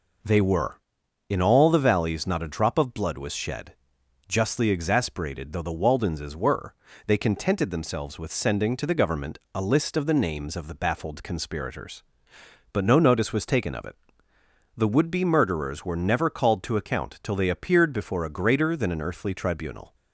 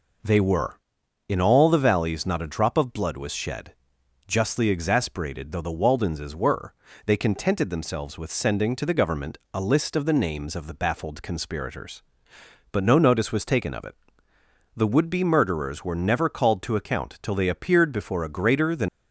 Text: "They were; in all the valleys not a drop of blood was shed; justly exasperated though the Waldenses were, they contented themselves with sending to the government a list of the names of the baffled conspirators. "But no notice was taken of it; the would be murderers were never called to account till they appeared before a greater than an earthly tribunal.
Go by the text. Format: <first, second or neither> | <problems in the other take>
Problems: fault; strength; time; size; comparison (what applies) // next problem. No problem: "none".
first | pauses between "government" and "a"; slight; at 9.3 s; 0.16 s long; slight in the first // stops before "an earthly tribunal"; at 18.8 s